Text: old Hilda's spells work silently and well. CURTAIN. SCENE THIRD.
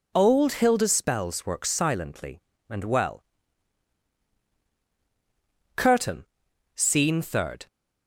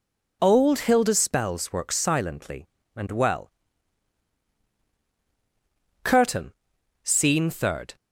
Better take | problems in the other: neither | none

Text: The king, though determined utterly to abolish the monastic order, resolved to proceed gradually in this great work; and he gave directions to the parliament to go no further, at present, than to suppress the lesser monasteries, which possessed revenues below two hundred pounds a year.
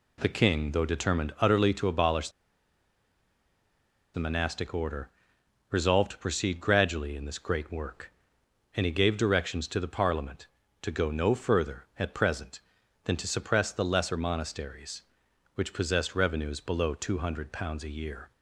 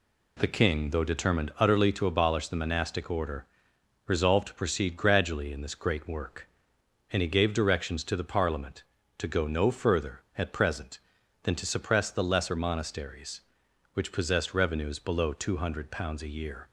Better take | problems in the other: second | pauses between "abolish" and "the"; strong; at 2.2 s; 1.8 s long

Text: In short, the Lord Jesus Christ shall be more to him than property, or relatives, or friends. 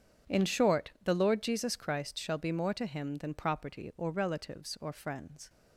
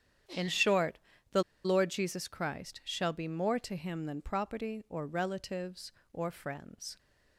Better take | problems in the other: first | starts louder than the rest; strong; until 1.8 s; 9.5 dB; strong in the first // pauses between "the" and "Lord"; slight; at 1.4 s; 0.22 s long

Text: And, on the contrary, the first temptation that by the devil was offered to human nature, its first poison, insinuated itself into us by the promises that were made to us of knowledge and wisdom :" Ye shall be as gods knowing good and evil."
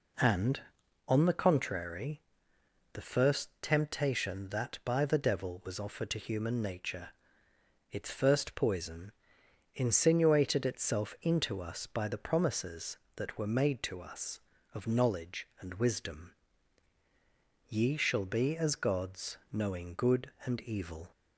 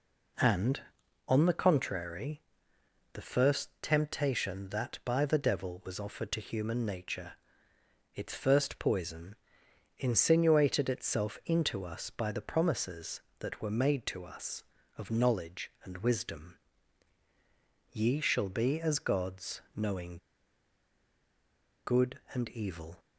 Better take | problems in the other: first | pauses between "knowing" and "good"; strong; at 20.1 s; 1.6 s long

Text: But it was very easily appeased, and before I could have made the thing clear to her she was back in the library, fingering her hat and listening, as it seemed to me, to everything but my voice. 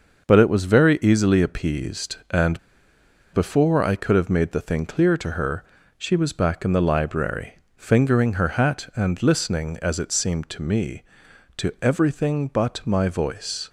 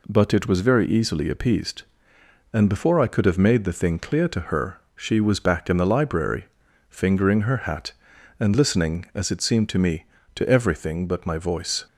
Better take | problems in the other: second | starts louder than the rest; until 1.3 s; 6 dB // pauses between "and" and "before"; noticeable; at 2.5 s; 0.75 s long // pauses between "her" and "she"; slight; at 5.6 s; 0.36 s long; slight in the second

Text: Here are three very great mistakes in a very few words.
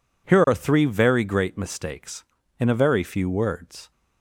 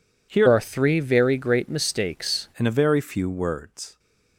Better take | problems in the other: first | changes voice from "are" to "mistakes"; from 0.4 to 2.4 s; 2.0 s long

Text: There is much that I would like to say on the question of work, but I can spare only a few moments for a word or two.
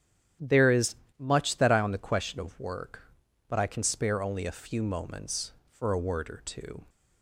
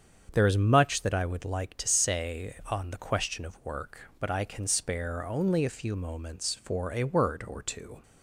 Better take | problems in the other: second | starts louder than the rest; strong; until 1.6 s; 9.5 dB; strong in the second // pauses between "is" and "much"; slight; at 0.9 s; 0.22 s long // skips "would like to say"; at 1.7 s

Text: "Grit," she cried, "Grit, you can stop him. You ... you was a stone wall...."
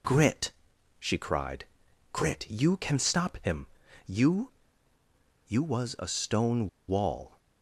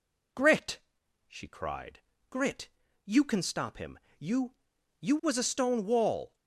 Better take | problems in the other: second | pauses between "stone" and "wall"; slight; at 6.6 s; 0.20 s long

